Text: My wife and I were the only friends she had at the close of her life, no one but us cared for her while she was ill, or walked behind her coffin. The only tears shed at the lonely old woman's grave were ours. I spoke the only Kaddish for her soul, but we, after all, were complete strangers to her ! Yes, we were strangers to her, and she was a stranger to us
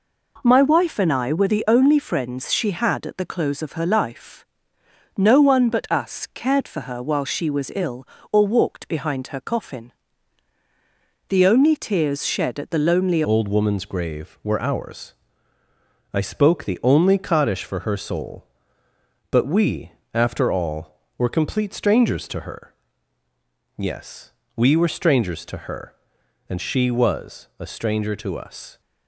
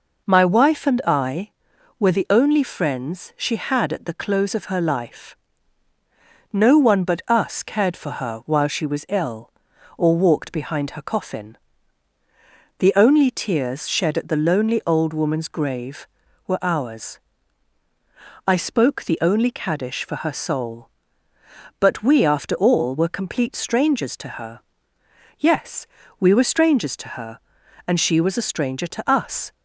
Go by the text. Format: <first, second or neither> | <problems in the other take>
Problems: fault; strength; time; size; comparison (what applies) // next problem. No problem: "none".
second | changes voice at "old"; from 13.2 s on; 15.6 s long